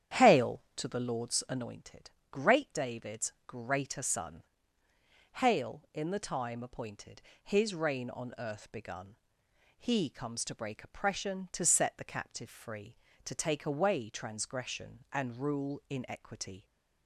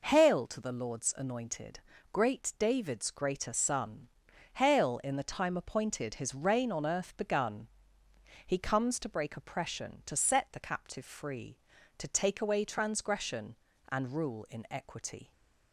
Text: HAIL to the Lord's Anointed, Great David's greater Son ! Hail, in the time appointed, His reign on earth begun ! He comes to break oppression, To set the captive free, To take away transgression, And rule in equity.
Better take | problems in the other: second | starts louder than the rest; strong; until 1.7 s; 9.5 dB

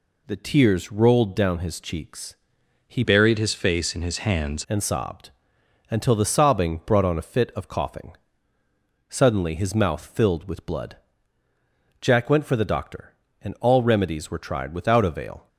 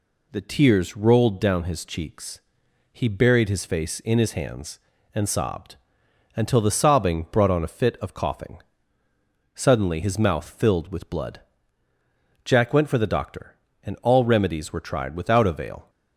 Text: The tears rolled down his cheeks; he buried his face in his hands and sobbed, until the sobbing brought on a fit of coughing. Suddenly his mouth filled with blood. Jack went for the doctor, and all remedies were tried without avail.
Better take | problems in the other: second | changes voice from "buried" to "hands"; from 3.0 to 4.6 s; 1.6 s long

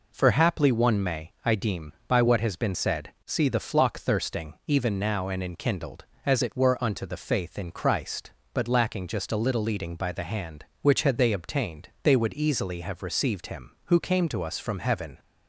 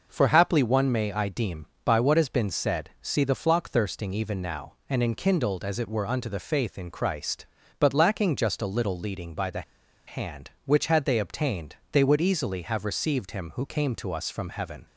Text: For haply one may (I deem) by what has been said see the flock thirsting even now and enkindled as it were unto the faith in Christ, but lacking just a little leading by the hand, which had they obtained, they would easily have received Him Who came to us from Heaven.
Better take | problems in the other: first | pauses between "the" and "hand"; at 9.6 s; 0.45 s long

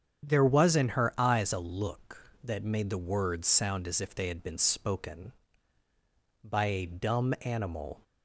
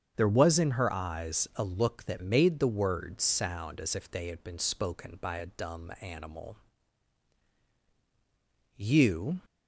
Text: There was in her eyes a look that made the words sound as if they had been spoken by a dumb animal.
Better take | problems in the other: first | starts louder than the rest; strong; until 1.1 s; 7.5 dB; strong in the first // goes on to say "You"; noticeable; from 8.7 s on; 0.64 s long

